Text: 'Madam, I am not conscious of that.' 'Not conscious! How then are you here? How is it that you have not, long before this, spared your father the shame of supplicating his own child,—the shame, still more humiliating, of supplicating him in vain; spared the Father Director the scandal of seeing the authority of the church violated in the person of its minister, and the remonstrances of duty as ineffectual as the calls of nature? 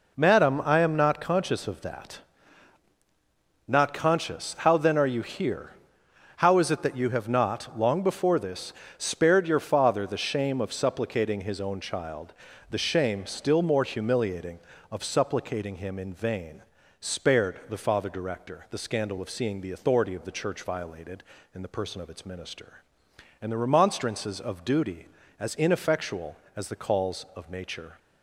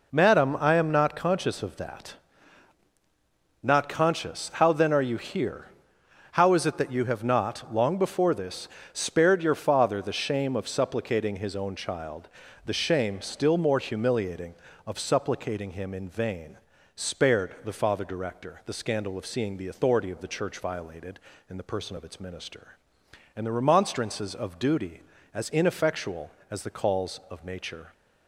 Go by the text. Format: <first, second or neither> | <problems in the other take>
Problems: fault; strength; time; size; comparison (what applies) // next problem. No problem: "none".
neither | none